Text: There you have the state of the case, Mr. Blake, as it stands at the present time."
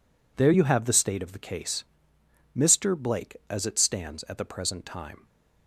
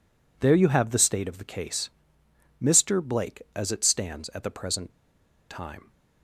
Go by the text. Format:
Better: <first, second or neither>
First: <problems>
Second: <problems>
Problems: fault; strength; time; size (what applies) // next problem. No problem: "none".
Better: first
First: none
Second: pauses between "present" and "time"; noticeable; at 4.8 s; 0.60 s long